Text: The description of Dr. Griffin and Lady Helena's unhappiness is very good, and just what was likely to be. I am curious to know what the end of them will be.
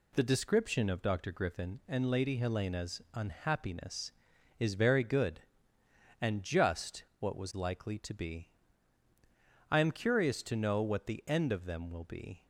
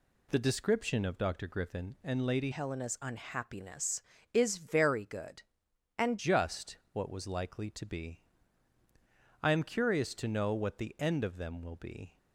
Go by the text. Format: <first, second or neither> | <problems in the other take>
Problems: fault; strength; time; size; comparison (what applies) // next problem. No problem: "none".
first | changes voice from "Helena's" to "and"; from 2.5 to 6.1 s; 3.6 s long // pauses between "just" and "what"; slight; at 6.7 s; 0.16 s long; slight in the first